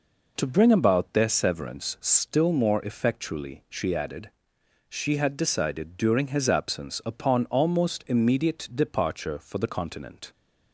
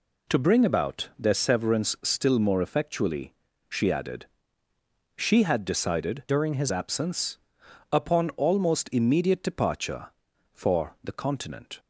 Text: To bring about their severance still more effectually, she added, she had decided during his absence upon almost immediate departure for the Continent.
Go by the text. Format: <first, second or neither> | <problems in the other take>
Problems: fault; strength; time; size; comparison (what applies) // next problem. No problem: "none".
first | changes voice from "during" to "his"; from 6.2 to 6.7 s; 0.5 s long // pauses between "absence" and "upon"; noticeable; at 7.3 s; 0.54 s long